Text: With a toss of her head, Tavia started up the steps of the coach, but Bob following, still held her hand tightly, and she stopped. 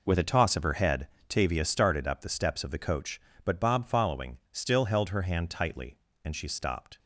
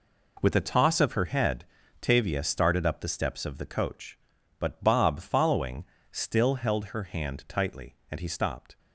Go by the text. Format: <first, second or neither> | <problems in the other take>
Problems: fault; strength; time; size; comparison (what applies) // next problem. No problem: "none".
first | says "he" for "she"; at 8.1 s